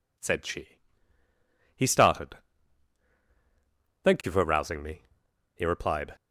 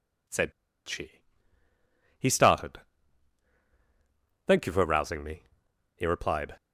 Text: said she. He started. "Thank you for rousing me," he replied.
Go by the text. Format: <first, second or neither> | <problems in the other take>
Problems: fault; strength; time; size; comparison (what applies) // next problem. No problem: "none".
first | pauses between "said" and "she"; slight; at 0.5 s; 0.35 s long